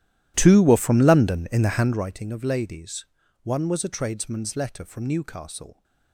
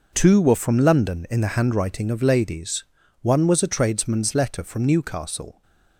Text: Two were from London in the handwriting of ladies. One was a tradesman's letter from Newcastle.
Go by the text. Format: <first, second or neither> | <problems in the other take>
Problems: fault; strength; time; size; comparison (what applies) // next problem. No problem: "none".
second | starts louder than the rest; strong; until 2.1 s; 13 dB